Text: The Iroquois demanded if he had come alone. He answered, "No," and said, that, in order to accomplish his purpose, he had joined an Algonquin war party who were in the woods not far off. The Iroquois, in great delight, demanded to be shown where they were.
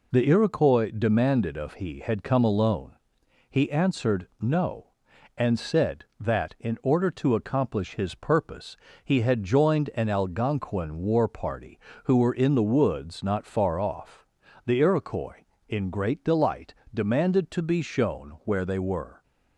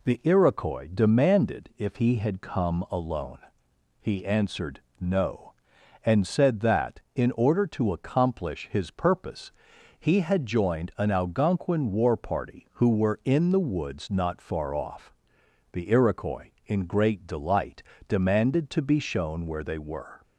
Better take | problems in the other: second | says "of" for "if"; at 1.5 s

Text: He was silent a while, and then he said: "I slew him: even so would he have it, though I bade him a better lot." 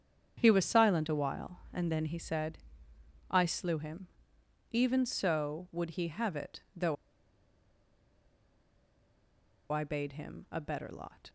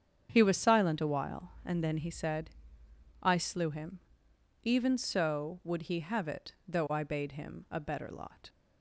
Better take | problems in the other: second | starts louder than the rest; strong; until 1.4 s; 8 dB; strong in the second // pauses between "though" and "I"; strong; at 6.9 s; 2.7 s long

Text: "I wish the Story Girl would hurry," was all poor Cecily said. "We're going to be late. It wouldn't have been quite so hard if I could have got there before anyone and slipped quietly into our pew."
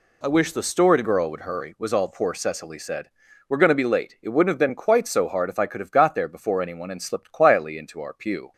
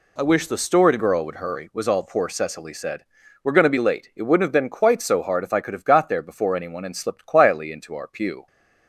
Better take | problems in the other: neither | none

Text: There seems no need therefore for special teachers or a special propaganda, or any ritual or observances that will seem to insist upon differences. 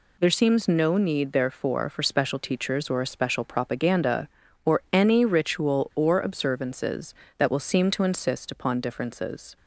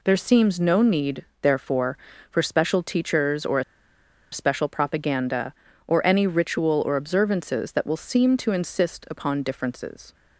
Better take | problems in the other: first | pauses between "need" and "therefore"; slight; at 1.2 s; 0.18 s long // pauses between "a" and "special"; noticeable; at 3.6 s; 0.68 s long

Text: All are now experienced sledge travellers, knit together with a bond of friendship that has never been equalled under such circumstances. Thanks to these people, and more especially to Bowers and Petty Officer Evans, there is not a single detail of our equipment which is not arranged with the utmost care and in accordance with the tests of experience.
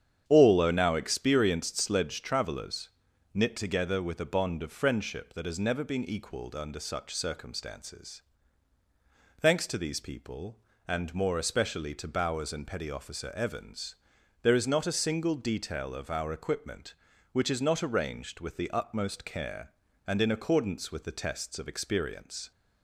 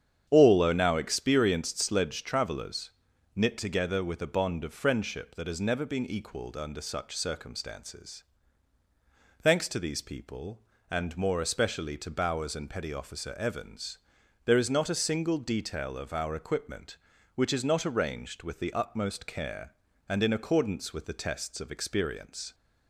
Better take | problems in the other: neither | starts louder than the rest; strong; the same in both

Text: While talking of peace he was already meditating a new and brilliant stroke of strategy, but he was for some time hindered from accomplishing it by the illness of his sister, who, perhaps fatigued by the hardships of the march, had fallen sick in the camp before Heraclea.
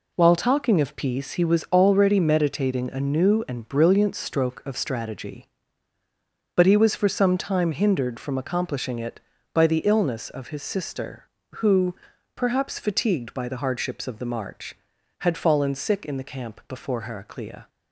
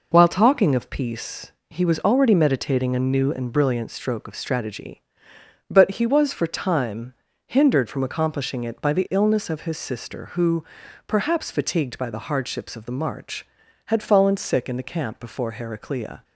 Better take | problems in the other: first | pauses between "peace" and "he"; slight; at 1.5 s; 0.18 s long // skips "some"; at 6.4 s // pauses between "time" and "hindered"; slight; at 7.1 s; 0.32 s long

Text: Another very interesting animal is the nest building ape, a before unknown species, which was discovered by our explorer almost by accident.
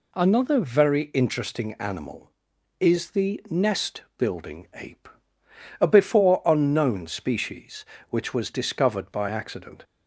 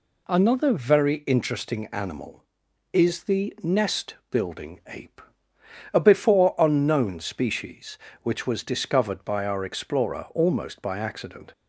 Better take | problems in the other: second | pauses between "nest" and "building"; slight; at 4.0 s; 0.16 s long; slight in the second // skips "our explorer almost by"; at 9.2 s

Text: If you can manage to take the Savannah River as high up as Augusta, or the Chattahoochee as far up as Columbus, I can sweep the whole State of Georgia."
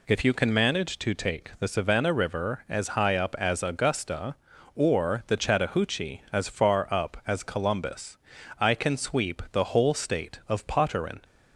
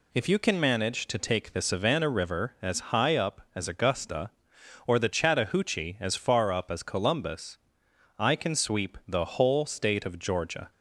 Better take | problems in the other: second | says "Potterin" for "Georgia"; at 10.6 s

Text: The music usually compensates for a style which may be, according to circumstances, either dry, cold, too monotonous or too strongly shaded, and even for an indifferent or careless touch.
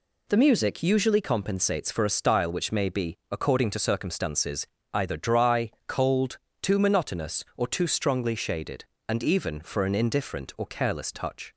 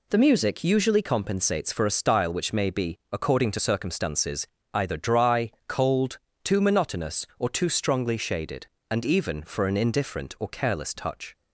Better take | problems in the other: neither | none

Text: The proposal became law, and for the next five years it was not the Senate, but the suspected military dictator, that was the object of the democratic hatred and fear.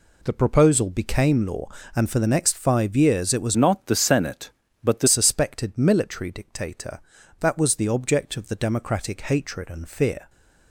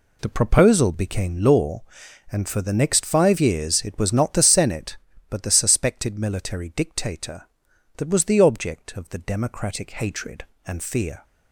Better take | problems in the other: second | changes voice from "not" to "the"; from 3.5 to 5.0 s; 1.5 s long

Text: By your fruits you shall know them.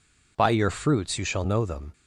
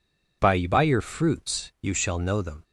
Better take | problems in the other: first | says "By" twice; at 0.6 s

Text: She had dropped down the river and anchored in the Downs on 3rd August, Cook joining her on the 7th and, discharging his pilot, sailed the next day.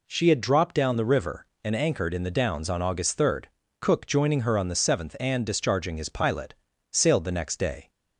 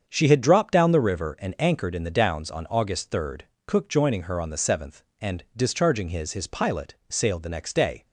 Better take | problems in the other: first | starts louder than the rest; strong; until 1.0 s; 7 dB // says "his" twice; at 6.3 s

